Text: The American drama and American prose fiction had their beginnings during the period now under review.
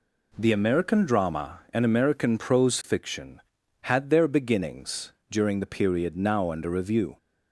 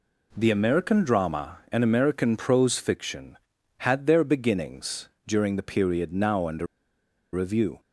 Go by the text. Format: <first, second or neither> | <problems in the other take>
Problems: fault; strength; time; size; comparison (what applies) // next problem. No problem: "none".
first | pauses between "beginnings" and "during"; slight; at 5.0 s; 0.18 s long; slight in the first // pauses between "under" and "review"; noticeable; at 6.6 s; 0.67 s long